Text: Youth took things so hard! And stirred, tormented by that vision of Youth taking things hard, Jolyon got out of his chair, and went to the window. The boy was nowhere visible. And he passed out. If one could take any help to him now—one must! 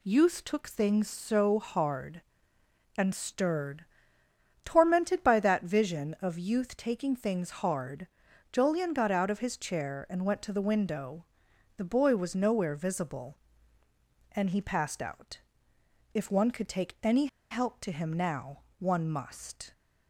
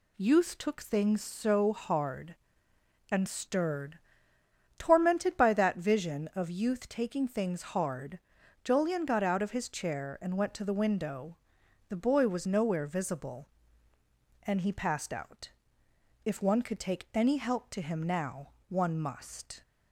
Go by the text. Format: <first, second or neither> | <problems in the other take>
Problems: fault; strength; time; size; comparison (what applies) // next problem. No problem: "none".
second | pauses between "any" and "help"; slight; at 17.2 s; 0.24 s long